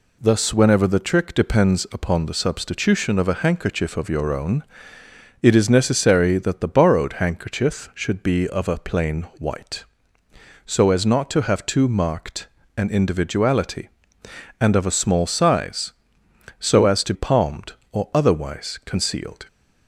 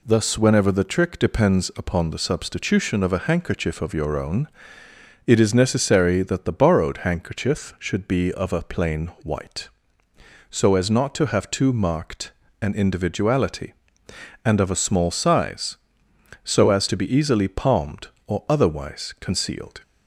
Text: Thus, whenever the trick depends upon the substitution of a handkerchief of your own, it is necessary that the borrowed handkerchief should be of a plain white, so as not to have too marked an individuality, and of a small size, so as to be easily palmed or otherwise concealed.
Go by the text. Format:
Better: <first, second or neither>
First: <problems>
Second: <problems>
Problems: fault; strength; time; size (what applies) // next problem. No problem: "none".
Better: second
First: pauses between "marked" and "an"; slight; at 12.4 s; 0.28 s long // skips "be easily"; at 17.1 s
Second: pauses between "marked" and "an"; slight; at 12.3 s; 0.28 s long